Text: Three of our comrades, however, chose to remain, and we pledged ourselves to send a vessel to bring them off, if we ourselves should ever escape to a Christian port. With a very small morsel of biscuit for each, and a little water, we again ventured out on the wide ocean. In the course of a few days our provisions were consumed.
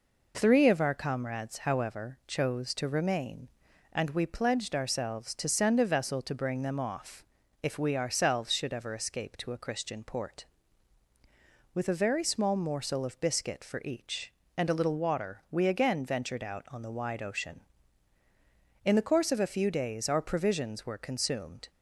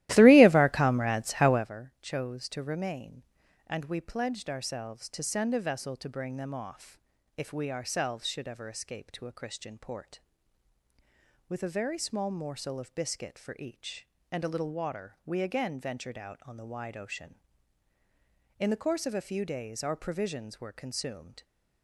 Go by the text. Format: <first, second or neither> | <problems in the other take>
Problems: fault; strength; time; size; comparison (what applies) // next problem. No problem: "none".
first | starts louder than the rest; strong; until 1.8 s; 15.5 dB